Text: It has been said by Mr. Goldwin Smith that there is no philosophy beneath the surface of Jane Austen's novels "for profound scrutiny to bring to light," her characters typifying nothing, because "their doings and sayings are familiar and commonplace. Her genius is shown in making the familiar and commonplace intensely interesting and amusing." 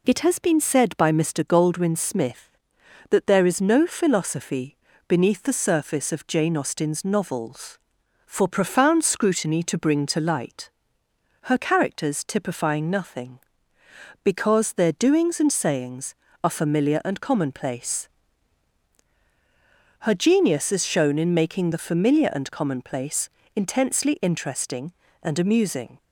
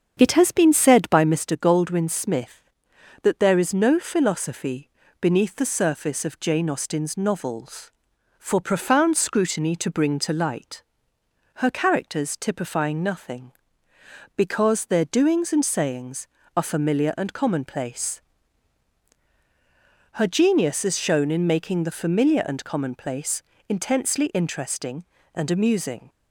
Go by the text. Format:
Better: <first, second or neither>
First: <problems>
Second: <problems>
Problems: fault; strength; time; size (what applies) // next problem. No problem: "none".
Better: first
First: pauses between "philosophy" and "beneath"; slight; at 4.7 s; 0.30 s long // pauses between "commonplace" and "intensely"; slight; at 23.3 s; 0.24 s long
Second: starts louder than the rest; strong; until 1.4 s; 7.5 dB // pauses between "philosophy" and "beneath"; slight; at 4.9 s; 0.30 s long // pauses between "commonplace" and "intensely"; slight; at 23.4 s; 0.24 s long